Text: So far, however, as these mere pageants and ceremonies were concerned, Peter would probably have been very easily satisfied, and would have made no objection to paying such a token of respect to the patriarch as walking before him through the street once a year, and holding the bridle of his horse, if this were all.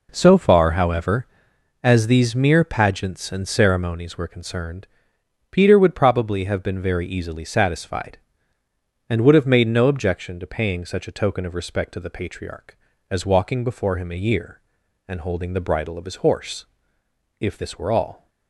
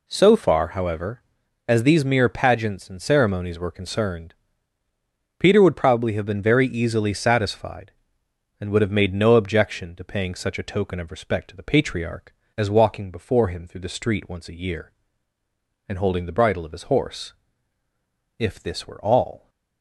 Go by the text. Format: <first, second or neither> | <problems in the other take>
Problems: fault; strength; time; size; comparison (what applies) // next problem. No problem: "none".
second | skips "through the street once"; at 14.1 s